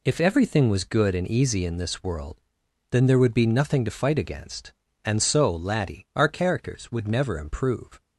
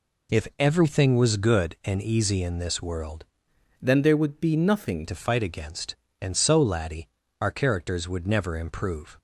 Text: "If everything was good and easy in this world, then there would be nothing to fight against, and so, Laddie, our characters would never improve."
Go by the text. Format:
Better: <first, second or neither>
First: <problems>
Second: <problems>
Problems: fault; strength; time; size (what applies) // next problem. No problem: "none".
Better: first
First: none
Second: changes voice from "then" to "nothing"; from 3.8 to 5.0 s; 1.2 s long